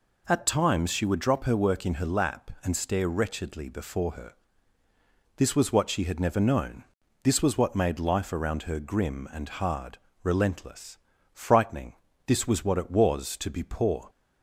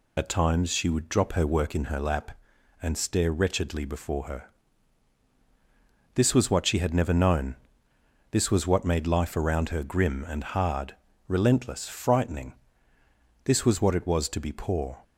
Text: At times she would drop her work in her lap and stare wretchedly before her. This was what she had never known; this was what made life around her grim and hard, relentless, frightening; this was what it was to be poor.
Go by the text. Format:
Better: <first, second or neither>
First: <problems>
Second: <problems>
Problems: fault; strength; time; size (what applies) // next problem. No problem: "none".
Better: first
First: none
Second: loses the start of "At"; at 0.1 s; 50 ms